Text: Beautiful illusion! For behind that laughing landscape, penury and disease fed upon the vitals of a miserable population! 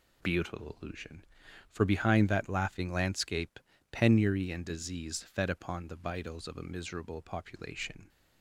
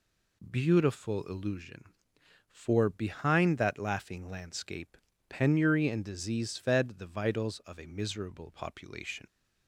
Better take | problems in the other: first | skips "upon"; at 6.9 s

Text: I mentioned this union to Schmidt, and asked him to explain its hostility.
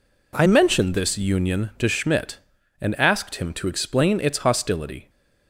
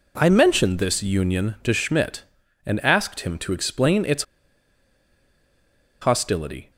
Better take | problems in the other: first | pauses between "its" and "hostility"; strong; at 4.2 s; 1.7 s long

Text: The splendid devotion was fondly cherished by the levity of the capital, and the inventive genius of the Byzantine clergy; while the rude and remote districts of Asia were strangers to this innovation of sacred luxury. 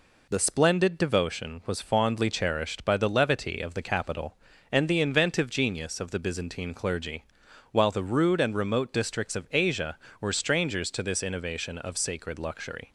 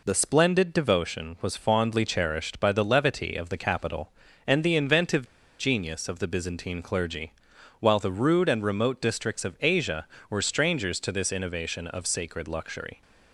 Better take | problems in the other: first | pauses between "inventive" and "genius"; slight; at 5.2 s; 0.34 s long

